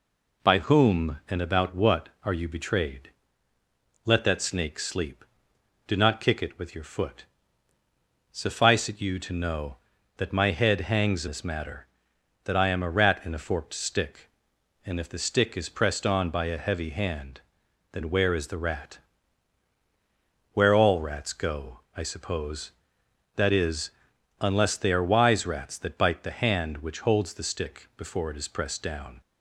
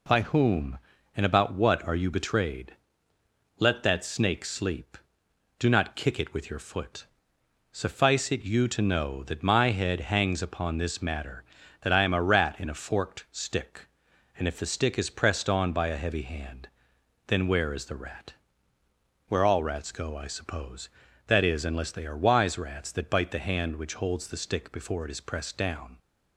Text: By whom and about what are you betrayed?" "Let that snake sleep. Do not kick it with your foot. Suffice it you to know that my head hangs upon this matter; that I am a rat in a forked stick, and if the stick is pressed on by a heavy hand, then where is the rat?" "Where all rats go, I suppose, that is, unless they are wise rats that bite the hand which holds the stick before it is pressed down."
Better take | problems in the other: second | skips "upon"; at 11.2 s

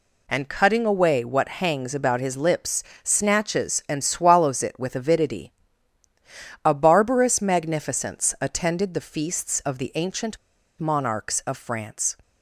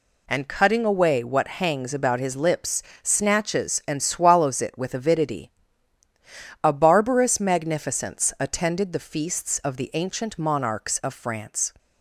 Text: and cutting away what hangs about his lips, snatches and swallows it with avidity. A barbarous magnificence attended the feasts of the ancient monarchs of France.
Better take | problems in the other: second | pauses between "ancient" and "monarchs"; at 10.3 s; 0.42 s long

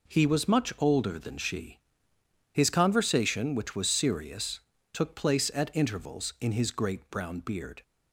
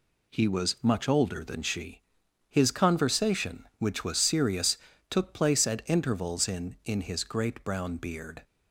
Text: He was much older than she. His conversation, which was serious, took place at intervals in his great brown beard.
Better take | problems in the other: first | says "in" twice; at 6.8 s

